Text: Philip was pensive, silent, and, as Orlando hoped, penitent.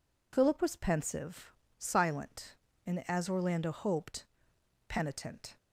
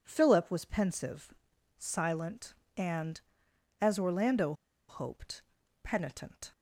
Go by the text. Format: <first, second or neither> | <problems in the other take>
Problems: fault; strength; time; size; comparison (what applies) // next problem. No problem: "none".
first | pauses between "Orlando" and "hoped"; slight; at 4.5 s; 0.35 s long